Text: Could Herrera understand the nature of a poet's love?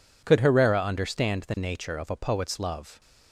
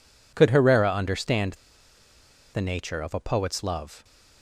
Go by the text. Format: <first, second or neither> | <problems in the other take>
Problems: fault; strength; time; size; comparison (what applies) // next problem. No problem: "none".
first | pauses between "understand" and "the"; at 1.5 s; 0.99 s long